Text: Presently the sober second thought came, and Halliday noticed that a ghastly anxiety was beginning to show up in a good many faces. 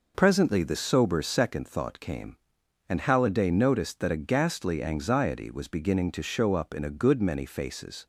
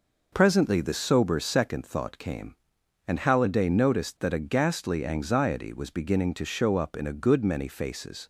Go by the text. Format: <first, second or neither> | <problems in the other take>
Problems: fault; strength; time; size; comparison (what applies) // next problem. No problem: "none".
neither | none